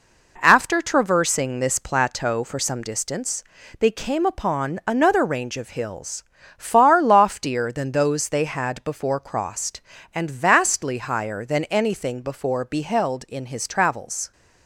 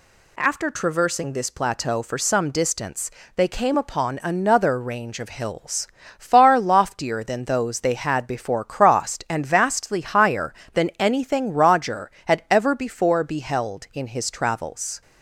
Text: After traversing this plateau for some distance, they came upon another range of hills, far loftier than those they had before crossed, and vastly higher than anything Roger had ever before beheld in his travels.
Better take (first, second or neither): second